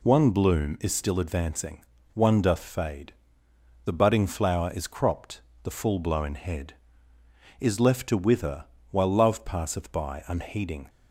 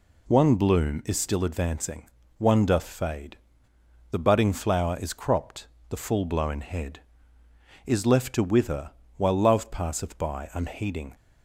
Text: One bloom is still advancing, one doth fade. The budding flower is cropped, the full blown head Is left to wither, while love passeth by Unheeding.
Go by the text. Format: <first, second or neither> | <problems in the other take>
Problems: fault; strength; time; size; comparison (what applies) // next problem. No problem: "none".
neither | none